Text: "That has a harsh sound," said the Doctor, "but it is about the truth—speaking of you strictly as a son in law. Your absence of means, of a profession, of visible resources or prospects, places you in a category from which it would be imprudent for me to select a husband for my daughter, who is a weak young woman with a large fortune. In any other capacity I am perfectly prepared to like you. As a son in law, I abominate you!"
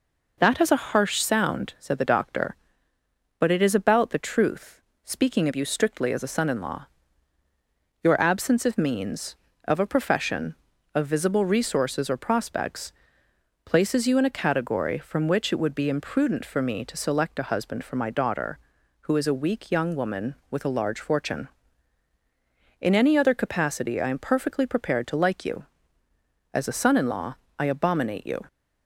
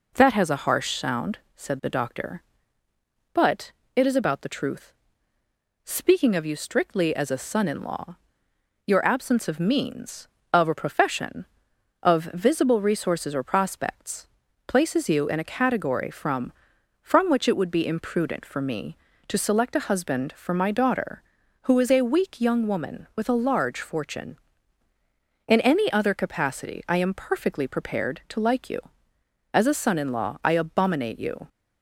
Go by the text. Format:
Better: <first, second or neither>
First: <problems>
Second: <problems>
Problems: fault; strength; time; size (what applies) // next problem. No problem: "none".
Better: first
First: none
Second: pauses between "but" and "it"; slight; at 3.7 s; 0.22 s long // says "from" twice; at 17.0 s